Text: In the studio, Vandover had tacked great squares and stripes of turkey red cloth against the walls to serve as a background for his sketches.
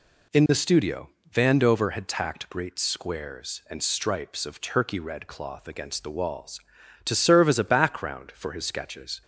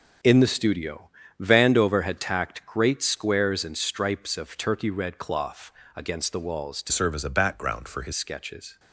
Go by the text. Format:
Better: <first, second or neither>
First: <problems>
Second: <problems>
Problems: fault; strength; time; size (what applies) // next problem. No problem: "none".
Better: first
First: none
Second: pauses between "cloth" and "against"; slight; at 5.7 s; 0.24 s long // changes voice from "serve" to "his"; from 6.9 to 8.1 s; 1.2 s long